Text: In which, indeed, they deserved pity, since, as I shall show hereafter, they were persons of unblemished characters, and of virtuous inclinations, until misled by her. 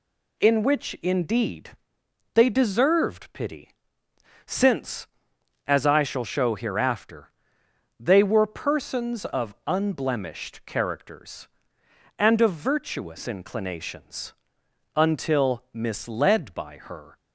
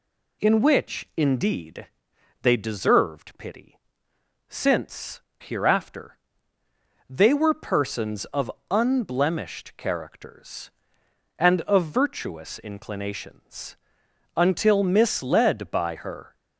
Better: first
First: none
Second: skips "as I shall show"; at 5.3 s // pauses between "of" and "unblemished"; slight; at 8.5 s; 0.20 s long

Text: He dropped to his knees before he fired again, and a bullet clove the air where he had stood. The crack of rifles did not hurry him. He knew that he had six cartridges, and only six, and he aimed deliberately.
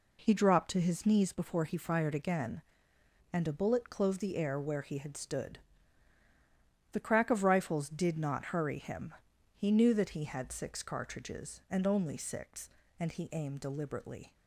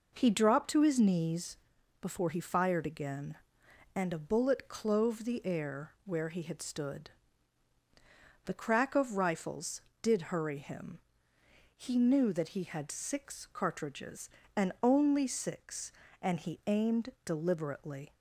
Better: first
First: none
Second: pauses between "knees" and "before"; at 1.5 s; 0.42 s long // skips "not"; at 10.2 s

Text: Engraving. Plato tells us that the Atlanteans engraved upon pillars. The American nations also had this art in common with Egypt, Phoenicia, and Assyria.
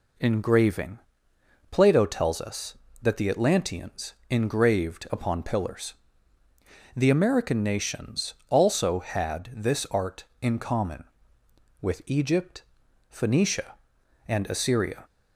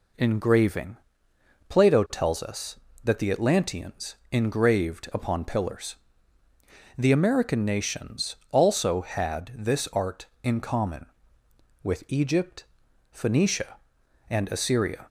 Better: neither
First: pauses between "Atlanteans" and "engraved"; slight; at 4.1 s; 0.16 s long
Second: pauses between "Atlanteans" and "engraved"; slight; at 4.1 s; 0.16 s long

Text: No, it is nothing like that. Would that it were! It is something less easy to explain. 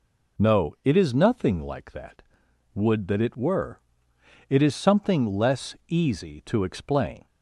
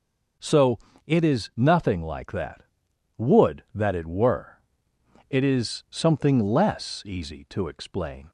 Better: first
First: none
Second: says "So" for "No"; at 0.3 s

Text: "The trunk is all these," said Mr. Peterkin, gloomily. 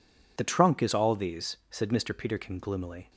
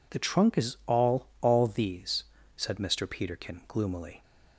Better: first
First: none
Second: says "all" twice; at 1.4 s

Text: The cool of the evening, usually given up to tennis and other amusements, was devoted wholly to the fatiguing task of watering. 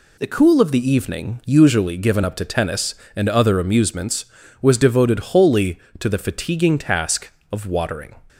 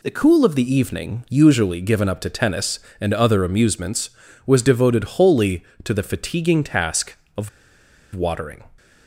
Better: first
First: none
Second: pauses between "of" and "watering"; noticeable; at 7.4 s; 0.66 s long

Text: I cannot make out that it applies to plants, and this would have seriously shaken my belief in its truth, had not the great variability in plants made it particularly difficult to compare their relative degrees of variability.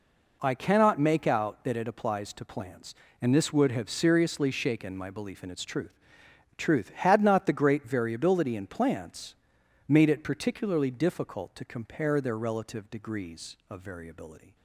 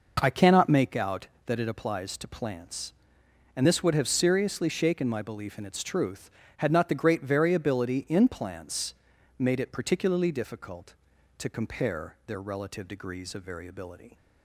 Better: second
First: says "truth" twice; at 6.5 s // pauses between "plants" and "made"; noticeable; at 9.3 s; 0.54 s long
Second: pauses between "plants" and "made"; at 8.9 s; 0.44 s long

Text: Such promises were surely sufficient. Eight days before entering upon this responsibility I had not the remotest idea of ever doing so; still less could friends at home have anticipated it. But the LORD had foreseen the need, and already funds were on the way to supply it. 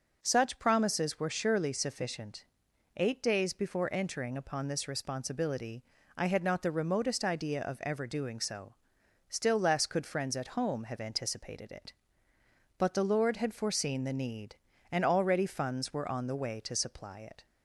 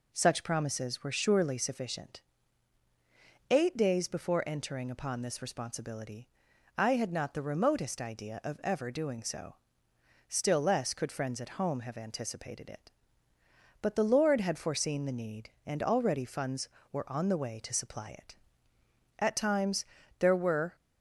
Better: first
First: pauses between "responsibility" and "I"; slight; at 5.8 s; 0.34 s long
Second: pauses between "responsibility" and "I"; noticeable; at 6.2 s; 0.46 s long // goes on to say "At times there were"; from 19.1 s on; 1.5 s long

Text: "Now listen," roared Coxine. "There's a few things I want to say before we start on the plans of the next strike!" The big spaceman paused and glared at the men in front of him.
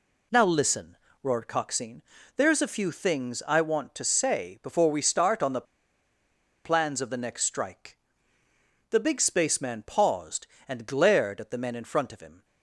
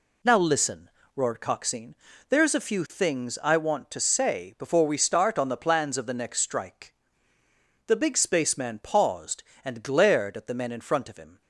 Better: second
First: pauses between "the" and "plans"; at 5.6 s; 1.0 s long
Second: none

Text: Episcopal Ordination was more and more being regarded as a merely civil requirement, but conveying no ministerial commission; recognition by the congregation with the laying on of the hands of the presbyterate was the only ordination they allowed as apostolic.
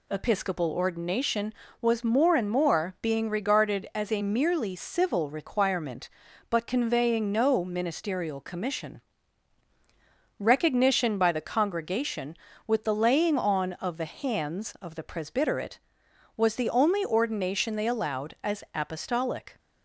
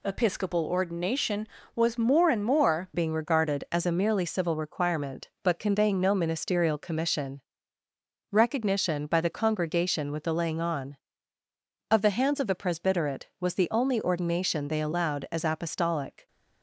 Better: first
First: none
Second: changes voice at "being"; from 2.9 s on; 13.3 s long

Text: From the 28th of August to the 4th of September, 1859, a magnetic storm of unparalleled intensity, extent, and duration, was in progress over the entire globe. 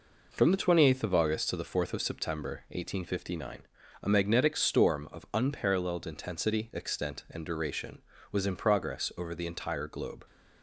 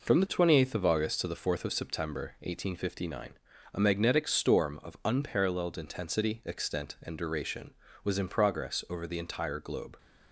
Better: neither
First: none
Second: none

